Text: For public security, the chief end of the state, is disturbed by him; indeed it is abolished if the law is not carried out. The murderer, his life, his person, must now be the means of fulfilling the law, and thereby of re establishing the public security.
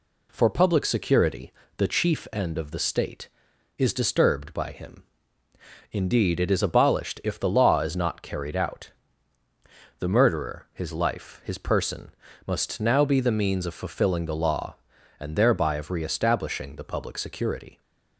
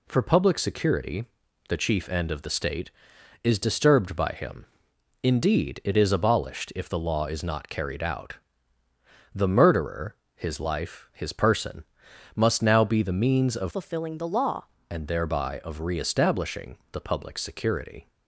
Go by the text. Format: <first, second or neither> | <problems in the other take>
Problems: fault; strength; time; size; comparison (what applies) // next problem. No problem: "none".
first | changes voice from "fulfilling" to "law"; from 13.7 to 14.6 s; 0.9 s long